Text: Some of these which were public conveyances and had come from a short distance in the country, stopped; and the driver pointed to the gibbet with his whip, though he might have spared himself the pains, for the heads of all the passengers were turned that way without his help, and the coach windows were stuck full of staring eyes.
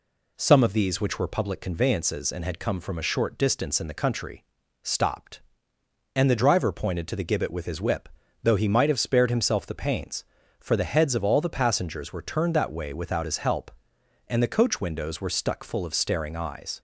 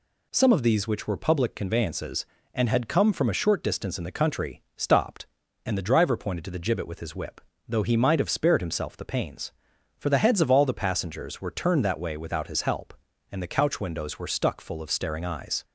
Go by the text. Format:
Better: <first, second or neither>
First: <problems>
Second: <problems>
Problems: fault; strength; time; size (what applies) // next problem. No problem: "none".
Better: first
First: none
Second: says "couch" for "coach"; at 13.4 s